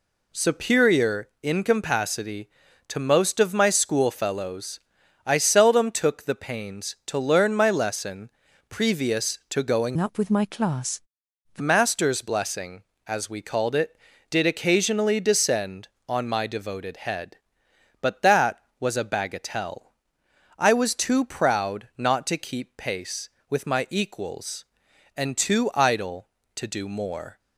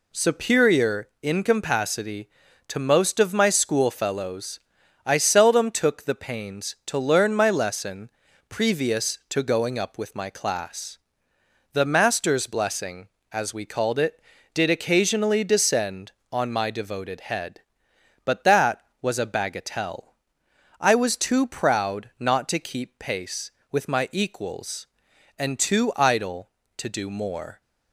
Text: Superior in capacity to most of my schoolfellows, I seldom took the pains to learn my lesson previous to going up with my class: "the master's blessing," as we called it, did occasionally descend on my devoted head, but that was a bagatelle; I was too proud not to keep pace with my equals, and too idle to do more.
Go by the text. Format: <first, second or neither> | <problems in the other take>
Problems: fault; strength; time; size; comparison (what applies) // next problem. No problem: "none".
second | pauses between "lesson" and "previous"; at 8.2 s; 0.40 s long; also in the second // changes voice from "up" to "the"; from 9.9 to 11.6 s; 1.7 s long